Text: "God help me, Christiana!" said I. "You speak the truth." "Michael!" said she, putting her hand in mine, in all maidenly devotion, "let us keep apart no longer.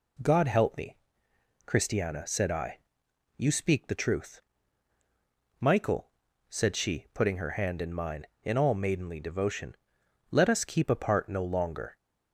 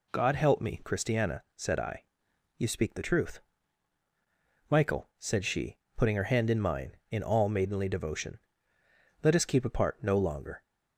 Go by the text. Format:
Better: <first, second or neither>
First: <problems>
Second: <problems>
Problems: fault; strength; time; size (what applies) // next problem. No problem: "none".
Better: neither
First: none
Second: none